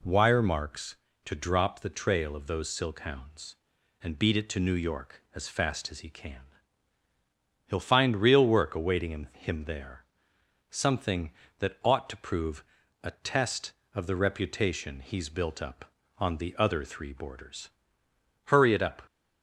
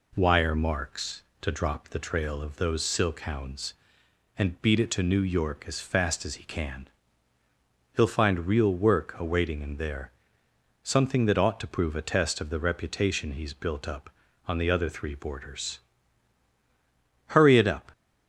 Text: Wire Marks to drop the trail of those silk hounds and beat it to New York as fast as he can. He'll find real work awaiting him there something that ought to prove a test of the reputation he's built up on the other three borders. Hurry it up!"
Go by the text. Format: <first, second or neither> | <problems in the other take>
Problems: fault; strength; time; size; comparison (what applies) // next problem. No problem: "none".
second | says "him" twice; at 9.3 s // pauses between "there" and "something"; noticeable; at 10.0 s; 0.70 s long; noticeable in the second // pauses between "prove" and "a"; at 12.6 s; 0.40 s long